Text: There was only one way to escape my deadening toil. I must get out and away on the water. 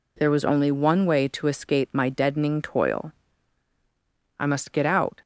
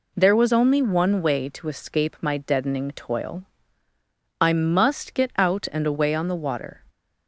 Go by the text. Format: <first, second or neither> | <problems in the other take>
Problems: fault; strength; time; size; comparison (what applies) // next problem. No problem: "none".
second | stops before "and away on the water"; at 5.2 s